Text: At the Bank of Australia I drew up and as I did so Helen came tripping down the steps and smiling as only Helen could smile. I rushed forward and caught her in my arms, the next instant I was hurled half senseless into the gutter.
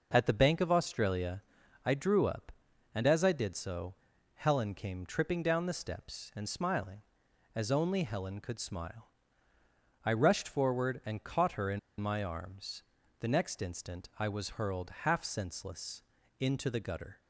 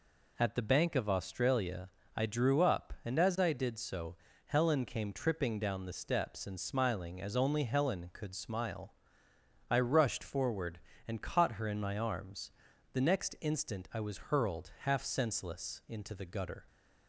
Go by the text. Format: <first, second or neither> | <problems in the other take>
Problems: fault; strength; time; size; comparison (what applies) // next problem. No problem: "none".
second | pauses between "Australia" and "I"; at 1.4 s; 0.44 s long; slight in the second // pauses between "so" and "Helen"; at 3.9 s; 0.40 s long; slight in the second // pauses between "in" and "my"; slight; at 11.7 s; 0.20 s long // pauses between "senseless" and "into"; slight; at 16.0 s; 0.36 s long